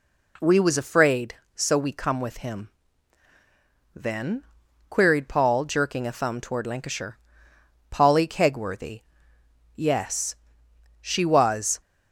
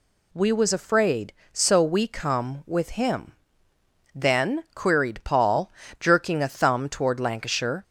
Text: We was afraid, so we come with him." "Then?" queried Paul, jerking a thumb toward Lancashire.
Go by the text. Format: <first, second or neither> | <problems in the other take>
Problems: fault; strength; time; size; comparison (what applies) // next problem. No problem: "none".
second | goes on to say "Polly Kegworthy Yes She was"; strong; from 7.8 s on; 3.9 s long